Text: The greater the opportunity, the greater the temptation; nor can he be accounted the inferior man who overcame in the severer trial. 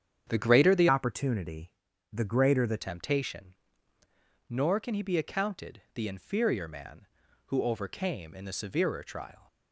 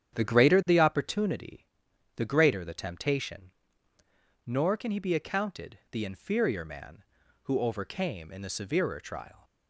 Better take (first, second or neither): second